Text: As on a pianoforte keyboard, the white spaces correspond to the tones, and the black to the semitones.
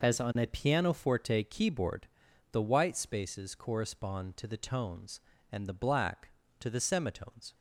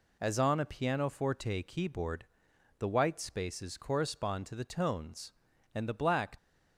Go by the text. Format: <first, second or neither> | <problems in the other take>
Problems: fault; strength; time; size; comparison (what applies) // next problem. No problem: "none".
first | stops before "to the semitones"; at 6.3 s